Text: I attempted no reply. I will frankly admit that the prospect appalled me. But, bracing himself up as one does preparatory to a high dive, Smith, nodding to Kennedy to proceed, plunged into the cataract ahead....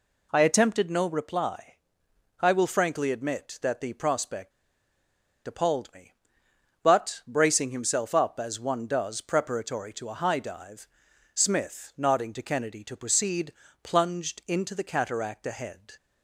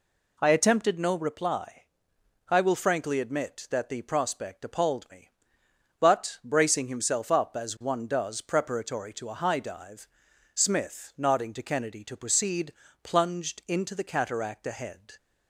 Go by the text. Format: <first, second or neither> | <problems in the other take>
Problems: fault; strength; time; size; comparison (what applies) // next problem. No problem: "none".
second | pauses between "prospect" and "appalled"; noticeable; at 4.5 s; 0.94 s long